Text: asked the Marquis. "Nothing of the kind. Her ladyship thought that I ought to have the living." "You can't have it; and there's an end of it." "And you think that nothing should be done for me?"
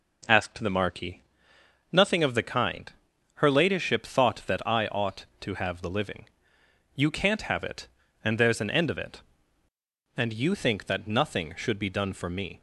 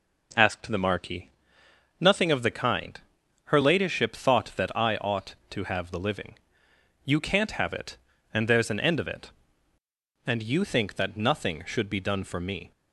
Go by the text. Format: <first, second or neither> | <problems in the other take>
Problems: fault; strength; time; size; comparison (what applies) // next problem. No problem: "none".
neither | none